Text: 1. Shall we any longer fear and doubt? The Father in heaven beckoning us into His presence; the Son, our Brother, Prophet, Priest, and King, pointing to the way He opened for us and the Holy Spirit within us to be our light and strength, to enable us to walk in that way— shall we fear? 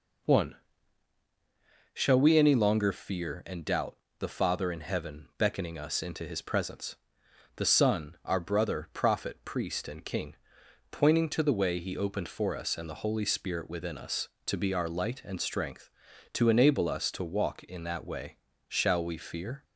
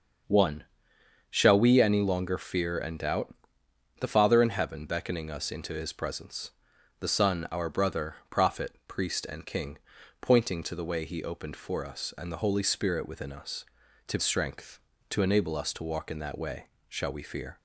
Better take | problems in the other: first | starts louder than the rest; until 1.9 s; 6.5 dB // skips "be our light and"; at 14.1 s

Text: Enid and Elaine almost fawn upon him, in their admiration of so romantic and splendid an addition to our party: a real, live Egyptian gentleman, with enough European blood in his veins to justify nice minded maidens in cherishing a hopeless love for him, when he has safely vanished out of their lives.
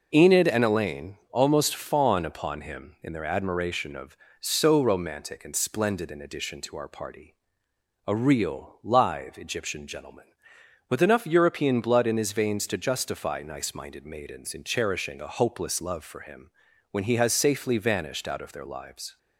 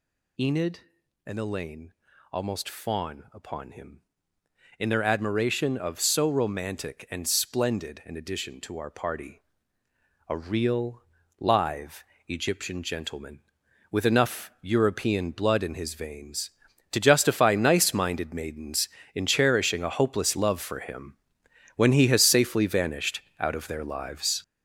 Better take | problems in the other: first | gets louder; strong; throughout; 8 dB // pauses between "Elaine" and "almost"; at 1.9 s; 0.40 s long // pauses between "live" and "Egyptian"; slight; at 12.0 s; 0.24 s long // pauses between "vanished" and "out"; slight; at 23.2 s; 0.18 s long

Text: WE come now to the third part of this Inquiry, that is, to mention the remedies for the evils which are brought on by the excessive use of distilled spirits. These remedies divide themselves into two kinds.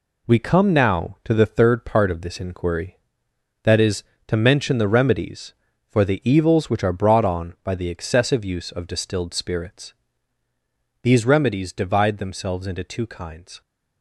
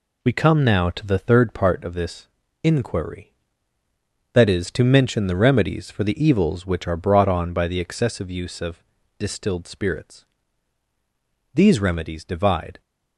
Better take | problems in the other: first | pauses between "this" and "Inquiry"; slight; at 2.2 s; 0.36 s long // pauses between "of" and "distilled"; slight; at 8.8 s; 0.34 s long // stops before "themselves into two kinds"; at 12.8 s

